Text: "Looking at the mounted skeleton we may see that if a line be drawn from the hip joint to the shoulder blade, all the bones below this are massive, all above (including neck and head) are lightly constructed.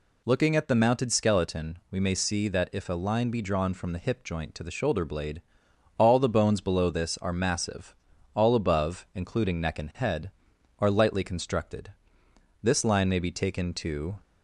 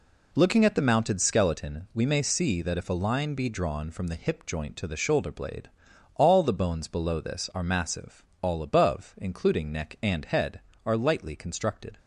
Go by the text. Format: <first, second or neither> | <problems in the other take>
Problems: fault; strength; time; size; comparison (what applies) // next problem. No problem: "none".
second | goes on to say "This line may be taken to"; from 12.6 s on; 1.5 s long